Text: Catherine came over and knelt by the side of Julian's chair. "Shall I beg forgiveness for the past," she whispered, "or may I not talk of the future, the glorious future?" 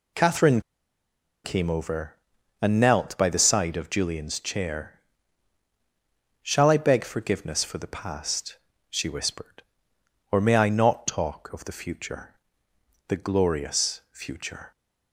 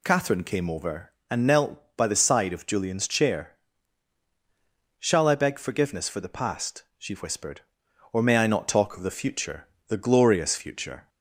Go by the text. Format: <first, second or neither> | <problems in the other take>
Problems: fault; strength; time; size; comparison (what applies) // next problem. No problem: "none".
second | pauses between "Catherine" and "came"; noticeable; at 0.6 s; 0.83 s long